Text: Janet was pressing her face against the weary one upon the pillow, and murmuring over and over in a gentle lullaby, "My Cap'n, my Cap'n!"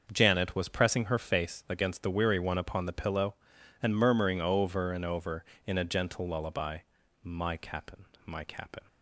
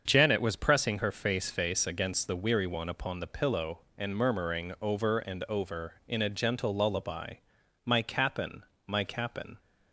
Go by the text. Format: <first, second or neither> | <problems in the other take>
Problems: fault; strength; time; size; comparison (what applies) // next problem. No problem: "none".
first | starts louder than the rest; until 1.0 s; 7 dB; also in the first // says "face" twice; at 1.5 s